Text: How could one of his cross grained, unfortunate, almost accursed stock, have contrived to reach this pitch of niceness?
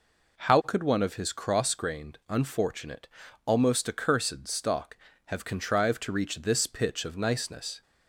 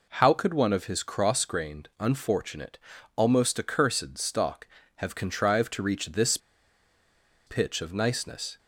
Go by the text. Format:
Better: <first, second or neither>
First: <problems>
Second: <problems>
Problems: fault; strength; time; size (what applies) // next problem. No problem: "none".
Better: first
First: none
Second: pauses between "this" and "pitch"; at 6.3 s; 1.0 s long